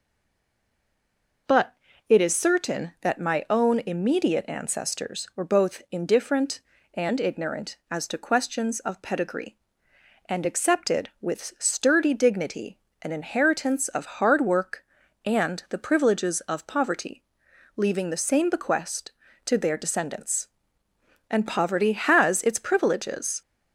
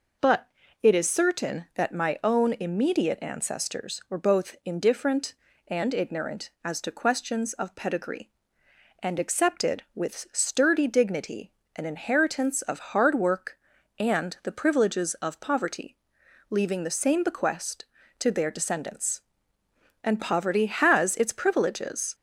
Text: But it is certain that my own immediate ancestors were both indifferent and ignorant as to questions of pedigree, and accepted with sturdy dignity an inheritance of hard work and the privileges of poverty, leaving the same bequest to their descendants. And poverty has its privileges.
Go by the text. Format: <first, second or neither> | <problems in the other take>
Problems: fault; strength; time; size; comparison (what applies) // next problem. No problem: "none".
second | stays silent before the first word; noticeable; until 1.4 s; 1.4 s long // pauses between "But" and "it"; slight; at 1.7 s; 0.36 s long; slight in the second // pauses between "dignity" and "an"; slight; at 12.7 s; 0.24 s long; slight in the second